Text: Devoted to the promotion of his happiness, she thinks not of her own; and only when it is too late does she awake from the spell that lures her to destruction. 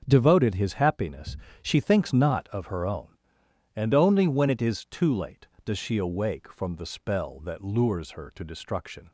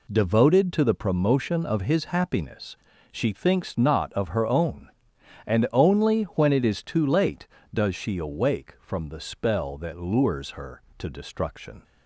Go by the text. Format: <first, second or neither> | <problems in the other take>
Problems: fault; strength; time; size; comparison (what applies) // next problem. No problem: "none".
second | starts louder than the rest; until 1.0 s; 6.5 dB // skips "to the promotion of"; at 0.5 s